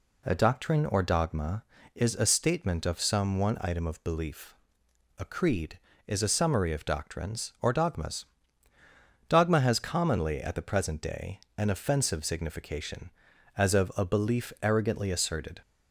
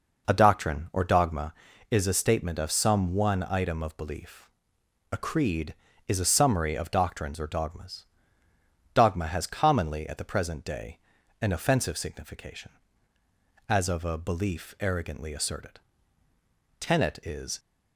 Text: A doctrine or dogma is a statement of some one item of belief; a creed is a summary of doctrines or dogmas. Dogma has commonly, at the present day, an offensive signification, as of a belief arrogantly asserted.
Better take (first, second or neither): first